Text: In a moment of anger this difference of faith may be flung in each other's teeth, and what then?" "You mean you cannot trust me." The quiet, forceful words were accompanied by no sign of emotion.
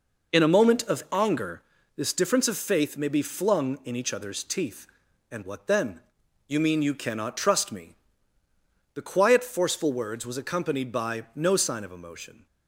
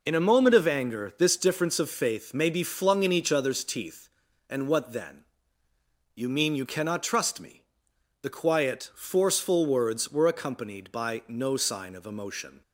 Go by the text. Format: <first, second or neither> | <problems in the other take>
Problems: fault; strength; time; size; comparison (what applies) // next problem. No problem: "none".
second | pauses between "anger" and "this"; slight; at 1.6 s; 0.34 s long // says "was" for "were"; at 10.2 s